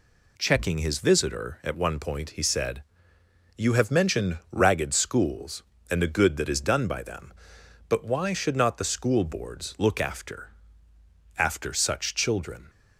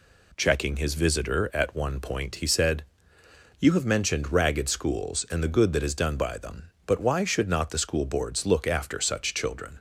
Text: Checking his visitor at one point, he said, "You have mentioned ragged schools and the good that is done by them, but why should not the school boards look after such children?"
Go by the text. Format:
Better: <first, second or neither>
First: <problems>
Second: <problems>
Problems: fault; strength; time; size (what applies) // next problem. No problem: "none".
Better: second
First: says "after" twice; at 11.3 s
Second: none